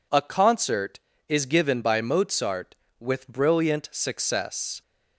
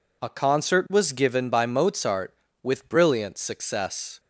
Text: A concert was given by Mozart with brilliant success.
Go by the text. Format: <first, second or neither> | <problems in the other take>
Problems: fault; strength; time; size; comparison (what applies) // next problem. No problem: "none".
second | says "is" for "was"; at 1.2 s